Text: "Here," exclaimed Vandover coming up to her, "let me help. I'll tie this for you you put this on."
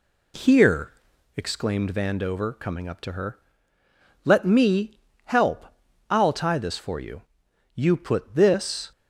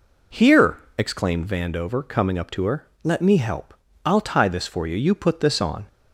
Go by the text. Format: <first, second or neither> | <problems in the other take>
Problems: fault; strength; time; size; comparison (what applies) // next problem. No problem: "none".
second | pauses between "me" and "help"; slight; at 4.9 s; 0.24 s long // pauses between "you" and "you"; noticeable; at 7.2 s; 0.52 s long // stops before "on"; at 8.9 s